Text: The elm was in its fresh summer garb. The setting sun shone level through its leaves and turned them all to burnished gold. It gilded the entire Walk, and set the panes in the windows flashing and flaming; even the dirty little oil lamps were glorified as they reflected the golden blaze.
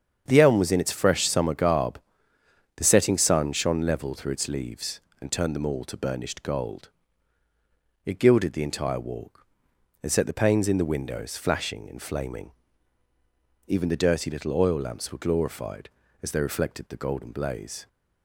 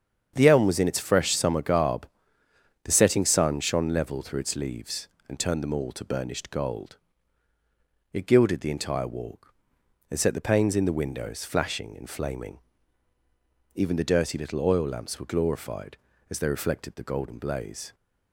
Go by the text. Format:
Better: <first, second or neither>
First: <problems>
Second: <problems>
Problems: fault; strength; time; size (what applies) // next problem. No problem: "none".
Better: neither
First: starts louder than the rest; strong; until 1.2 s; 7.5 dB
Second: starts louder than the rest; strong; until 1.3 s; 7.5 dB